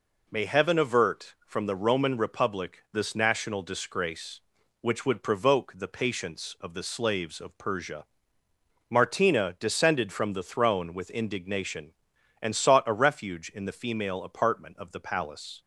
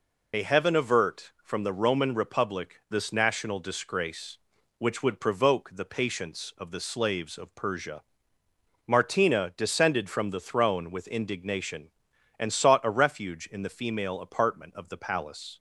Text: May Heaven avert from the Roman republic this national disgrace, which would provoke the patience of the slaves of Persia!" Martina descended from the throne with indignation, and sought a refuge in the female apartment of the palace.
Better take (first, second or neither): first